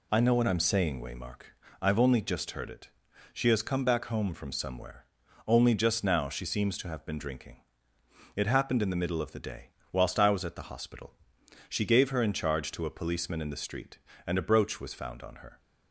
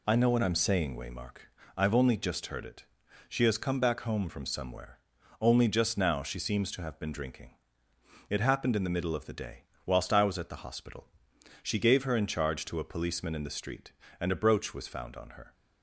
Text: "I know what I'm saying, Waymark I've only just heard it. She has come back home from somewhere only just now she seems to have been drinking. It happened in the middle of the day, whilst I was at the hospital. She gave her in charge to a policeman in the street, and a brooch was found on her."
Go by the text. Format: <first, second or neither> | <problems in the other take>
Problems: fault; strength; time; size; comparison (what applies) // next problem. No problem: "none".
neither | pauses between "Waymark" and "I've"; slight; the same in both // pauses between "somewhere" and "only"; the same in both